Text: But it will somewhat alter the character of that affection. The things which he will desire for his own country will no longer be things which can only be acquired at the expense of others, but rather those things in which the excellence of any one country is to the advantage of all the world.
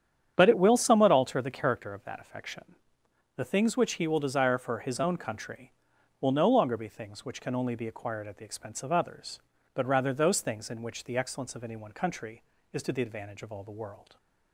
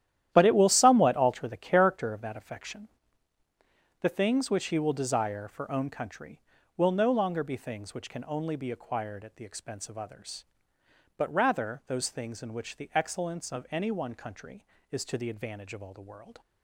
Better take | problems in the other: first | starts louder than the rest; strong; until 1.3 s; 11.5 dB; strong in the first // skips "his"; at 5.7 s

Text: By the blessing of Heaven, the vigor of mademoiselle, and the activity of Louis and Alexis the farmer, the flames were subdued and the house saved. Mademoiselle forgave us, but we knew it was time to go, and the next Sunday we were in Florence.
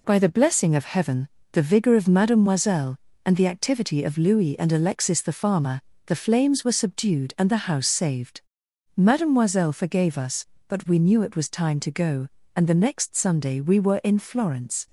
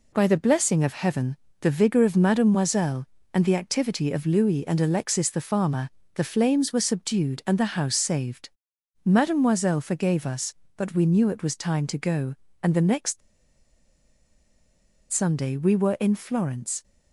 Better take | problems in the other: first | pauses between "next" and "Sunday"; strong; at 13.2 s; 1.9 s long

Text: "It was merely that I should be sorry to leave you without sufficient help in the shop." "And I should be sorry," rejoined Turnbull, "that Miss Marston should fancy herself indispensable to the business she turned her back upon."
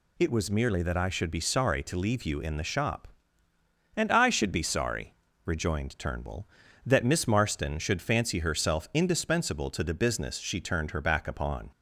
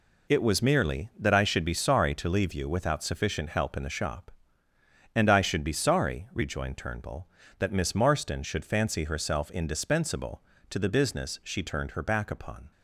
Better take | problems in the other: second | skips "without sufficient help"; at 2.3 s

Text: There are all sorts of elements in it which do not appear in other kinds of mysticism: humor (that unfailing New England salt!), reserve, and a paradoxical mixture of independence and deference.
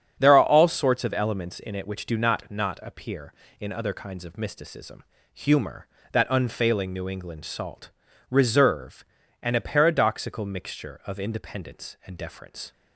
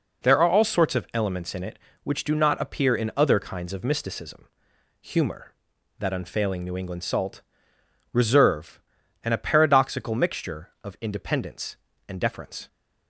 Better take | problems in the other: second | starts louder than the rest; strong; until 1.2 s; 8 dB // says "not" twice; at 2.4 s

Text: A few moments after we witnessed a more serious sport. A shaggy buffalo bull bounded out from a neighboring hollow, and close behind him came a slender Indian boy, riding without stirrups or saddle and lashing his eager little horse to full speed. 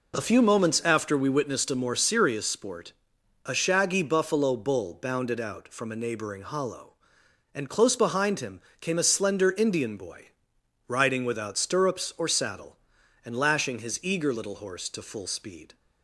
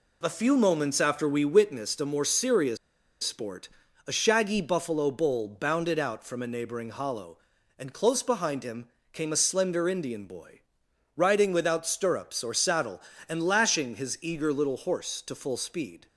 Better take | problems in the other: first | pauses between "serious" and "sport"; noticeable; at 2.7 s; 0.46 s long // pauses between "him" and "came"; slight; at 8.8 s; 0.24 s long; slight in the first

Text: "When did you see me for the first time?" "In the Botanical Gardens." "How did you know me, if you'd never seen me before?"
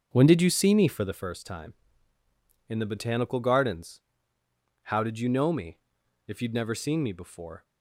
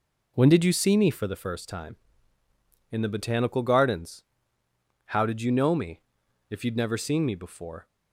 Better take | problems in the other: second | starts louder than the rest; until 1.2 s; 6.5 dB

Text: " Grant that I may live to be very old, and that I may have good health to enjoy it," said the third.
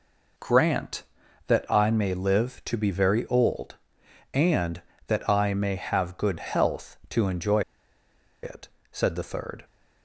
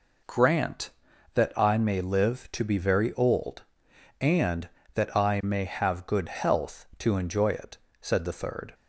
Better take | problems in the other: second | pauses between "enjoy" and "it"; noticeable; at 7.6 s; 0.82 s long

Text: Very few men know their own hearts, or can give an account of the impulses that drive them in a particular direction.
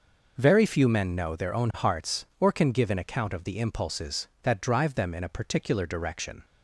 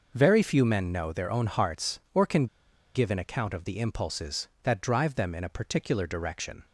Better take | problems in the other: first | pauses between "can" and "give"; noticeable; at 2.4 s; 0.47 s long

